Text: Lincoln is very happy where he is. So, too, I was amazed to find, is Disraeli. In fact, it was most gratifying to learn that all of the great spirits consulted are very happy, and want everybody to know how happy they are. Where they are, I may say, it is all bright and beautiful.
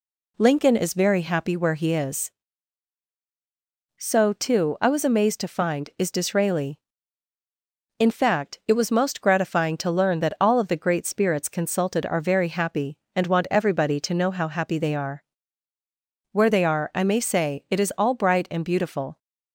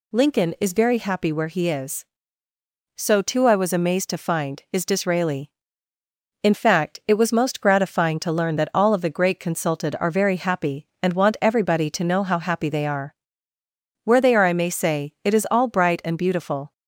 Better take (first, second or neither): first